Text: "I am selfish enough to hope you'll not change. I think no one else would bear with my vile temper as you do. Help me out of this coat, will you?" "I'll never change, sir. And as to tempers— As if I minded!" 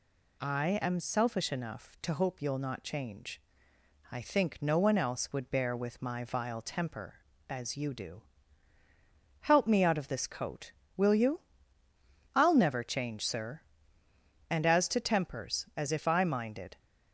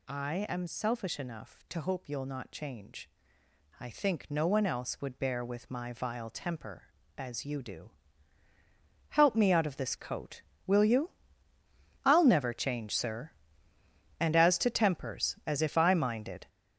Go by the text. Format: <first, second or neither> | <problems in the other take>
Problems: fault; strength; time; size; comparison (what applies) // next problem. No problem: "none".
first | gets louder; strong; throughout; 8 dB